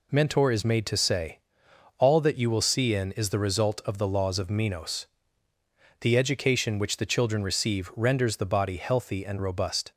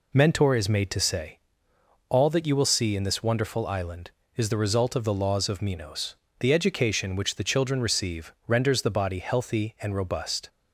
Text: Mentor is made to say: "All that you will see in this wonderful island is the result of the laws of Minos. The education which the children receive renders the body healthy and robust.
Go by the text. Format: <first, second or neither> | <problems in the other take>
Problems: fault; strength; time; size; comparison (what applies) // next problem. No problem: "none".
second | skips "this wonderful island"; at 3.1 s